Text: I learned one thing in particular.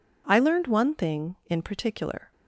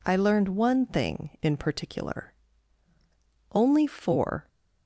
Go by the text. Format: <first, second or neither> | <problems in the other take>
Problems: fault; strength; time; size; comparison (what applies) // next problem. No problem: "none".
first | goes on to say "Only four"; noticeable; from 3.5 s on; 0.94 s long